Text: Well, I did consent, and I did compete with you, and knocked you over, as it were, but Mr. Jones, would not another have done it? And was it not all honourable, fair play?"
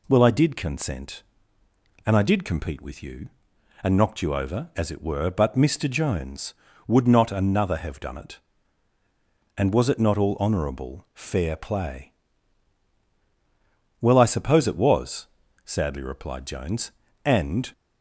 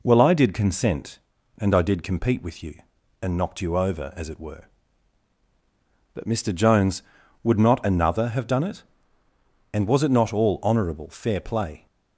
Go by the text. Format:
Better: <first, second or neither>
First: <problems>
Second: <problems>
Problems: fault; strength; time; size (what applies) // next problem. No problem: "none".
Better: second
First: goes on to say "Well I suppose it was sadly replied Jones and"; strong; from 14.0 s on; 3.7 s long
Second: none